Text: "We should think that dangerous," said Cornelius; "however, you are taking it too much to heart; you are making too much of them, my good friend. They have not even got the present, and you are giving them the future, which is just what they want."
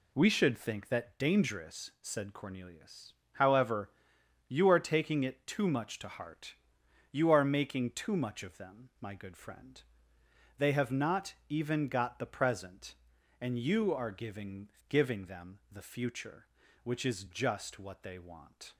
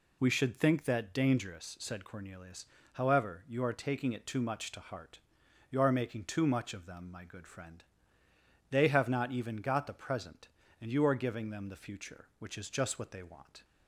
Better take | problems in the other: second | pauses between "not" and "even"; slight; at 11.3 s; 0.16 s long // says "giving" twice; at 14.8 s

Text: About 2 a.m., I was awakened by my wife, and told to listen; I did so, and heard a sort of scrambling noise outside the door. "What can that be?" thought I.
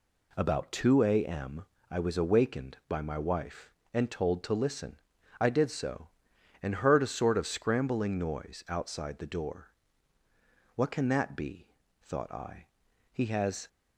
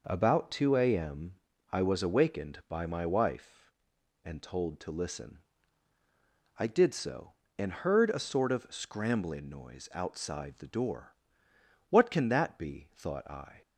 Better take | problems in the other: second | goes on to say "He has"; from 13.1 s on; 0.56 s long

